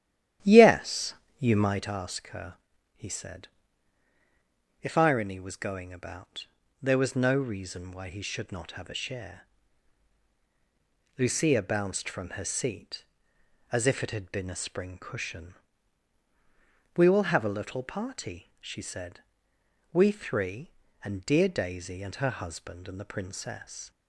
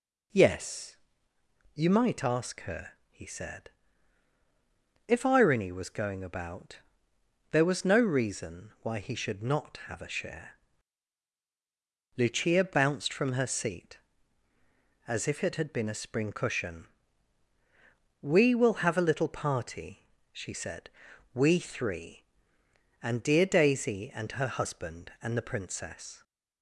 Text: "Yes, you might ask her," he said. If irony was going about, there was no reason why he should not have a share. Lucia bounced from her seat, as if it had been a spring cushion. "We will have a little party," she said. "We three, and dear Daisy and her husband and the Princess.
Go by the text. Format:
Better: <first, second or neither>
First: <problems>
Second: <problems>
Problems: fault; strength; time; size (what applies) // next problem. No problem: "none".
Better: second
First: starts louder than the rest; strong; until 1.9 s; 11.5 dB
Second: none